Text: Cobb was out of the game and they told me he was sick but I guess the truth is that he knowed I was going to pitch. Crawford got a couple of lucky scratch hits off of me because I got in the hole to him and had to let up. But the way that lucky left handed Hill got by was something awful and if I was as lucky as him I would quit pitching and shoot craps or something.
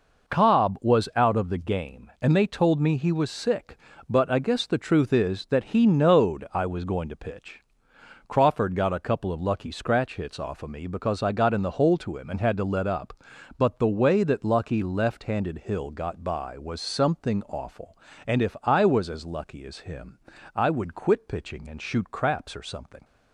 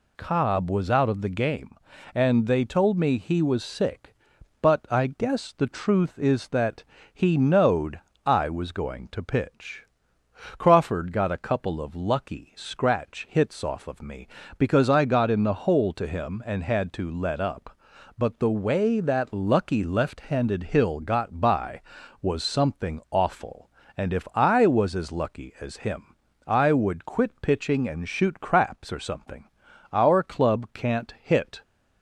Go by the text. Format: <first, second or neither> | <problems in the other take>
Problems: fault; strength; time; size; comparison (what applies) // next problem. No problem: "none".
first | pauses between "that" and "he"; slight; at 6.8 s; 0.30 s long // pauses between "knowed" and "I"; slight; at 7.9 s; 0.26 s long // pauses between "him" and "I"; slight; at 26.1 s; 0.32 s long; slight in the first // goes on to say "Our club can't hit"; strong; from 29.9 s on; 1.7 s long